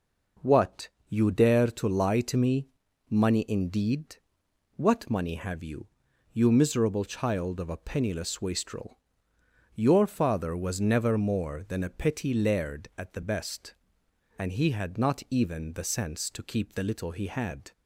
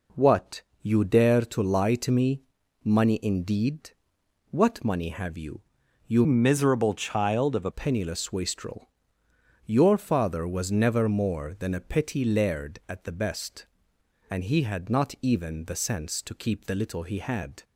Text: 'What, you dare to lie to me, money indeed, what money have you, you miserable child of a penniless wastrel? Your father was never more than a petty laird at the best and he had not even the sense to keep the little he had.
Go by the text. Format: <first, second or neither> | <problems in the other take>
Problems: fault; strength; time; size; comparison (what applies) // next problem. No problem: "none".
first | changes voice from "miserable" to "a"; from 6.2 to 7.6 s; 1.4 s long